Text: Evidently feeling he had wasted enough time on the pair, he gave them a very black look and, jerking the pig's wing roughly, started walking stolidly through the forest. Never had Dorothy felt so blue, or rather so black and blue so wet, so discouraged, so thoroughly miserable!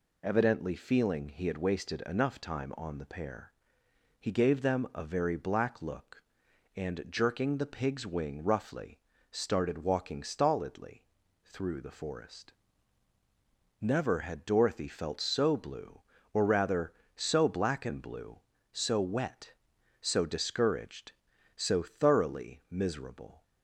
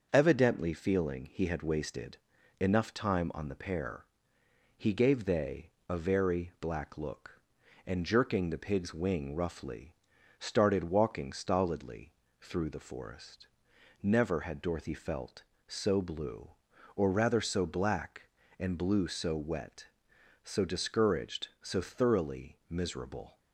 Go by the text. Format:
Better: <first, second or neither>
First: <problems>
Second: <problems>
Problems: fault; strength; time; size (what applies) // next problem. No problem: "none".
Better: first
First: pauses between "stolidly" and "through"; at 11.0 s; 0.40 s long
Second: starts louder than the rest; until 1.1 s; 6.5 dB // pauses between "wasted" and "enough"; at 2.1 s; 0.42 s long // says "they" for "them"; at 5.2 s // pauses between "stolidly" and "through"; slight; at 12.1 s; 0.30 s long